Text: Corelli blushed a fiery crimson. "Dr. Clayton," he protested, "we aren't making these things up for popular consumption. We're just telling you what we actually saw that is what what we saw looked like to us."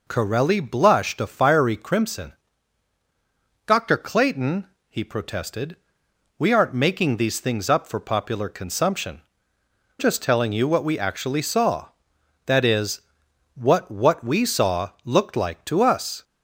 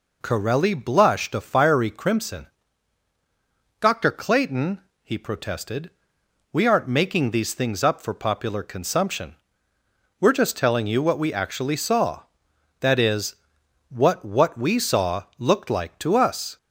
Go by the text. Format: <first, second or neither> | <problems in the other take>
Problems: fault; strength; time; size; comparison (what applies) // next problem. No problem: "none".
second | skips "We're"; at 9.5 s // pauses between "is" and "what"; noticeable; at 13.0 s; 0.54 s long; noticeable in the second